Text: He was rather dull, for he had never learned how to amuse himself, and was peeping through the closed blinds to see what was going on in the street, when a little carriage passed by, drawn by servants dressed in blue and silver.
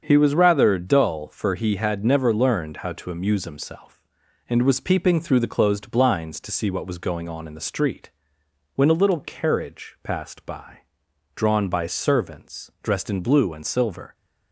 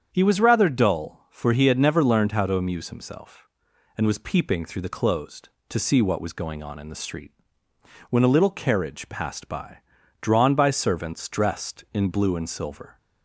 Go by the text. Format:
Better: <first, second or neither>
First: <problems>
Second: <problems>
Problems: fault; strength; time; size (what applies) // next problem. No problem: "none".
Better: first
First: starts louder than the rest; until 1.0 s; 7 dB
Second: starts louder than the rest; strong; until 1.1 s; 8 dB // skips "blinds"; at 5.5 s